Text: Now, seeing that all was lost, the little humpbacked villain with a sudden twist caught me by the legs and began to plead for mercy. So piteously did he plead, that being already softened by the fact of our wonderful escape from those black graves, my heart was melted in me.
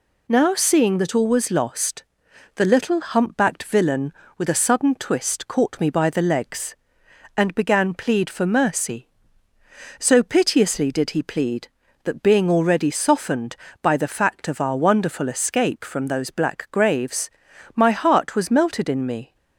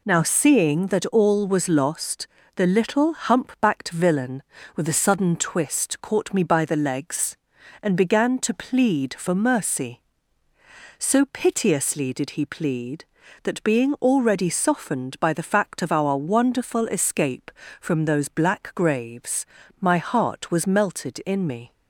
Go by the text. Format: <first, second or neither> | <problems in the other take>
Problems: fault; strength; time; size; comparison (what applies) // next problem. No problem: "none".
second | skips "to"; at 7.9 s